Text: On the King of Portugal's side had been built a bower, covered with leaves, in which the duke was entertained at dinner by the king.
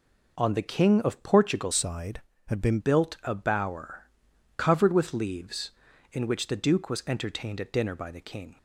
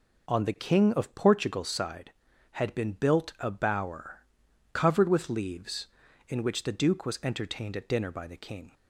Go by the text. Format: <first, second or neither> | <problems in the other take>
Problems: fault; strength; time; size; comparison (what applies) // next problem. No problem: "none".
second | changes voice from "side" to "been"; from 1.7 to 2.7 s; 1.0 s long